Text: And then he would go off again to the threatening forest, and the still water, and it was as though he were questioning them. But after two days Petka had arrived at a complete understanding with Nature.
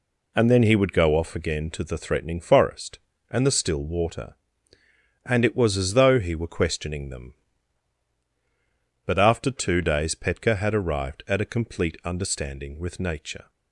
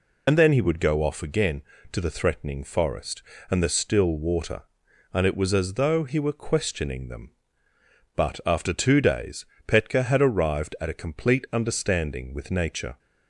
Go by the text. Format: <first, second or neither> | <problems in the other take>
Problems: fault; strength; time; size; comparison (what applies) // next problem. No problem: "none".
first | loses the start of "And"; at 0.2 s; 60 ms // pauses between "days" and "Petka"; slight; at 9.4 s; 0.22 s long